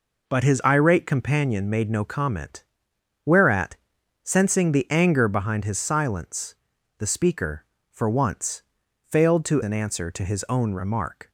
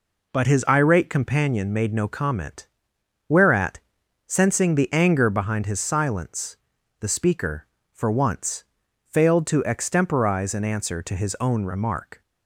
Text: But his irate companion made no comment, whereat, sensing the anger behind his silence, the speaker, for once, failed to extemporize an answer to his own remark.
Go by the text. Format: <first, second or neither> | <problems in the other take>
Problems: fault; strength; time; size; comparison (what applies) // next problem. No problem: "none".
second | skips "extemporize"; at 9.6 s